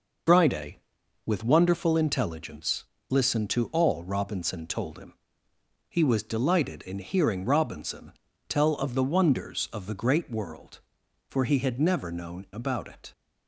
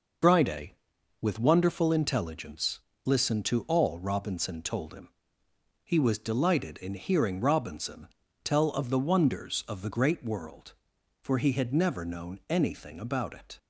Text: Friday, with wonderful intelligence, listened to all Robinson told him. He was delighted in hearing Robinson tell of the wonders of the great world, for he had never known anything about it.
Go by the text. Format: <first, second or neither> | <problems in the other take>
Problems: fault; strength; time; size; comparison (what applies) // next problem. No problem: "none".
second | pauses between "Robinson" and "tell"; at 8.1 s; 0.38 s long; also in the second // skips "anything"; at 12.4 s